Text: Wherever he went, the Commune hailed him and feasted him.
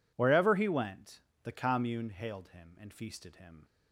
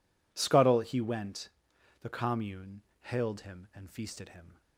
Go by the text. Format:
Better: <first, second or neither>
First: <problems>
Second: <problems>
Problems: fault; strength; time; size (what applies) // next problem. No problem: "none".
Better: first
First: none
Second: says "Scuttle" for "Wherever"; at 0.3 s // pauses between "Commune" and "hailed"; slight; at 2.8 s; 0.20 s long